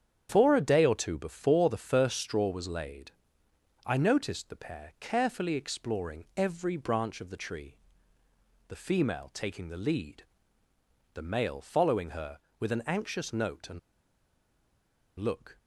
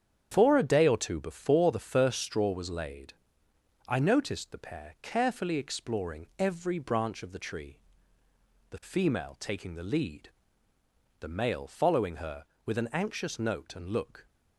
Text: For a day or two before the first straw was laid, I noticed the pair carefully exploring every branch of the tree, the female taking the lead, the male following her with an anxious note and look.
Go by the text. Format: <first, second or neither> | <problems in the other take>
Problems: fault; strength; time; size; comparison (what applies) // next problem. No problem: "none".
second | starts louder than the rest; strong; until 1.3 s; 8.5 dB; strong in the second // pauses between "and" and "look"; strong; at 13.7 s; 1.4 s long